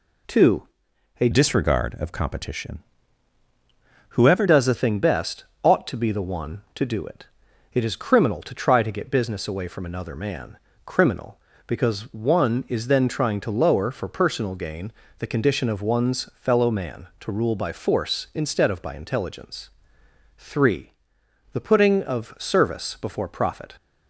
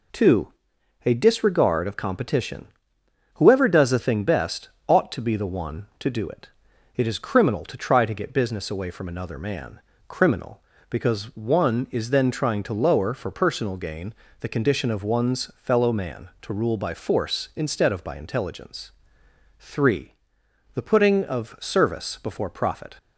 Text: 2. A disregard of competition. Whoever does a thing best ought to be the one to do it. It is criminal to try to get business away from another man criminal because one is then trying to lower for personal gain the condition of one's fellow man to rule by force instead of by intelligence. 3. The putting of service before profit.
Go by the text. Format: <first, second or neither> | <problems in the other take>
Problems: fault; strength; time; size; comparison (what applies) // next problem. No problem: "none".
second | changes voice from "disregard" to "Whoever"; from 1.3 to 4.4 s; 3.1 s long // pauses between "best" and "ought"; slight; at 5.4 s; 0.18 s long; slight in the second // pauses between "man" and "criminal"; slight; at 10.5 s; 0.28 s long; slight in the second // pauses between "gain" and "the"; slight; at 14.9 s; 0.26 s long; slight in the second